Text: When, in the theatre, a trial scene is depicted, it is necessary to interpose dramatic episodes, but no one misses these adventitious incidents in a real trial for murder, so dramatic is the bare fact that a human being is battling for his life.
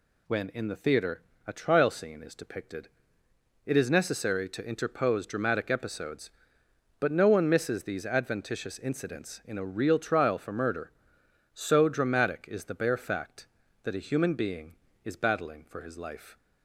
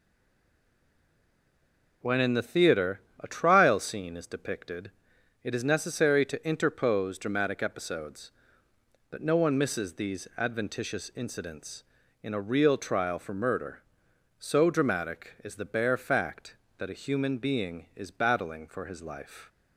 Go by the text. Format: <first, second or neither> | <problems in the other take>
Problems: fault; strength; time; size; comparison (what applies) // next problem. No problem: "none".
first | stays silent before the first word; noticeable; until 2.0 s; 2.0 s long